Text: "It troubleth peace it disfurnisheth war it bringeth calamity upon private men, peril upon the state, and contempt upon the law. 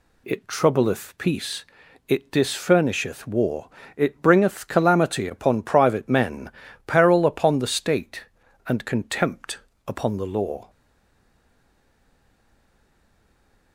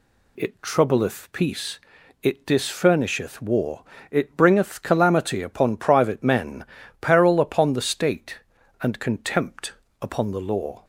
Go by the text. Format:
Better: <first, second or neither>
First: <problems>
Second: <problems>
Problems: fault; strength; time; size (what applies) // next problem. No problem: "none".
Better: second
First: pauses between "peace" and "it"; at 1.6 s; 0.42 s long // pauses between "war" and "it"; slight; at 3.6 s; 0.30 s long // pauses between "contempt" and "upon"; slight; at 9.5 s; 0.28 s long // stays silent after the last word; strong; from 10.6 s on; 3.1 s long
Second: pauses between "peace" and "it"; at 1.8 s; 0.42 s long // pauses between "war" and "it"; slight; at 3.8 s; 0.30 s long // pauses between "contempt" and "upon"; slight; at 9.7 s; 0.28 s long